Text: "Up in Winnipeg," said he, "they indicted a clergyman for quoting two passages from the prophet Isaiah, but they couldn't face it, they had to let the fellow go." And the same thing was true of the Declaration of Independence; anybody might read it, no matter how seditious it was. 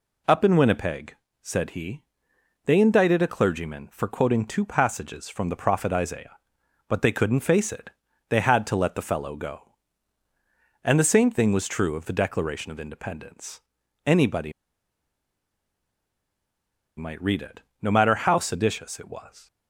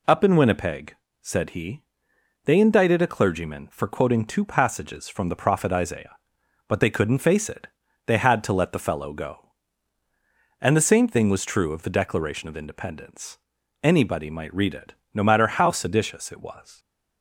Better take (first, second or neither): second